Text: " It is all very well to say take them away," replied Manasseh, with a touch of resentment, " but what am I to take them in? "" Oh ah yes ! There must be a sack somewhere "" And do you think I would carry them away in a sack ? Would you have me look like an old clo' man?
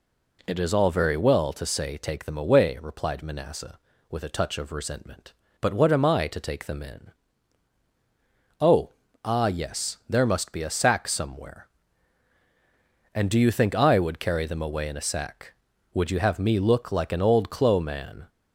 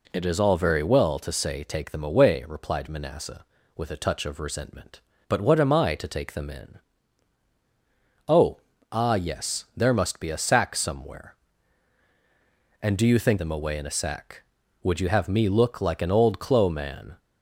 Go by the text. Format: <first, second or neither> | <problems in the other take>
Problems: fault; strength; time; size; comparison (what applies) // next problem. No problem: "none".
first | pauses between "Oh" and "ah"; slight; at 8.6 s; 0.32 s long; slight in the first // skips "I would carry"; at 13.3 s